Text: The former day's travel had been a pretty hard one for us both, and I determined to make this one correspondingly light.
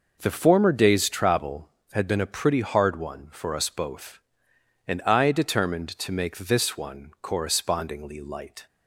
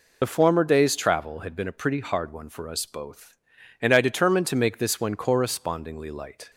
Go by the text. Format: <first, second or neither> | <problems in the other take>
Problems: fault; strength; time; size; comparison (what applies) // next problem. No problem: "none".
first | loses the start of "The"; at 0.2 s; 60 ms